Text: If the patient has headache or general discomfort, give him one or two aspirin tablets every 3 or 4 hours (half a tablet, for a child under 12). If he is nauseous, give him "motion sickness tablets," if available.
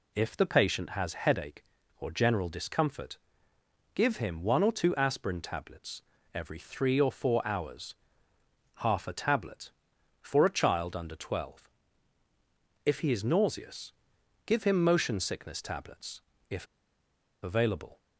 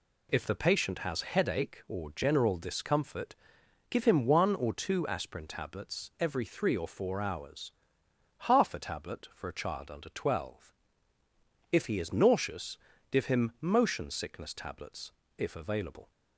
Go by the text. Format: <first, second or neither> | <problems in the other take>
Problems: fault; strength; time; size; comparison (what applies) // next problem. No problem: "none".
second | pauses between "tablets" and "every"; slight; at 6.0 s; 0.32 s long // pauses between "if" and "available"; noticeable; at 16.6 s; 0.77 s long